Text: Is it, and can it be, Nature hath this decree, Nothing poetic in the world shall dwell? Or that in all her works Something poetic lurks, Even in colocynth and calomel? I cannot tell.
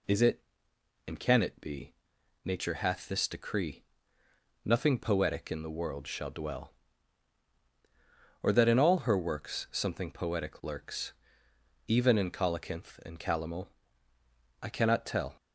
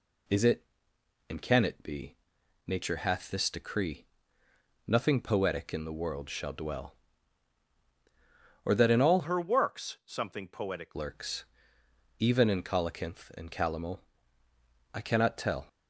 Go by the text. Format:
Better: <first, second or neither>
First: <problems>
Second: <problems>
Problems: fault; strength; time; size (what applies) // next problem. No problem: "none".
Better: first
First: none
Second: changes voice from "her" to "poetic"; from 9.2 to 10.9 s; 1.7 s long